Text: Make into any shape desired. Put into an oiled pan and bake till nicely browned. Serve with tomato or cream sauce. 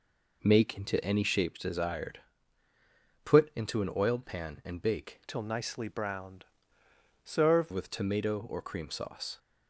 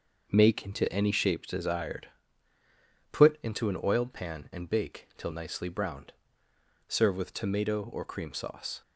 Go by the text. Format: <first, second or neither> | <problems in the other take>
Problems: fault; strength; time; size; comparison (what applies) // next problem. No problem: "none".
second | changes voice from "till" to "Serve"; from 5.2 to 7.7 s; 2.5 s long